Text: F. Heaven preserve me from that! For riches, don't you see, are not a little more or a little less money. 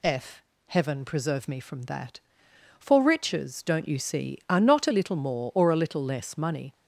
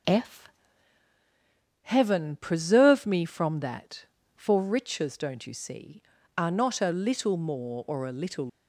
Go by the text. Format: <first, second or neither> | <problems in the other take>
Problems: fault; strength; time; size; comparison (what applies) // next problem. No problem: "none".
first | stops before "less money"; at 8.4 s